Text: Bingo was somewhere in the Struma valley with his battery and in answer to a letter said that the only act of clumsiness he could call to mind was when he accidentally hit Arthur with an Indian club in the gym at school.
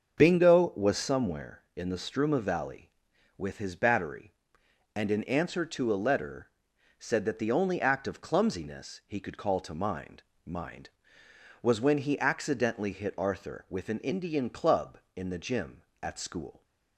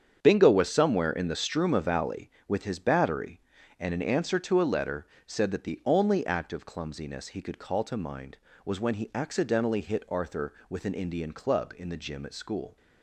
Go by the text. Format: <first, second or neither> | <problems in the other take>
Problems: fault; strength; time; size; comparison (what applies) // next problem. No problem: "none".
second | starts louder than the rest; until 1.2 s; 6.5 dB; strong in the second // pauses between "letter" and "said"; noticeable; at 6.4 s; 0.50 s long; slight in the second // says "mind" twice; at 10.4 s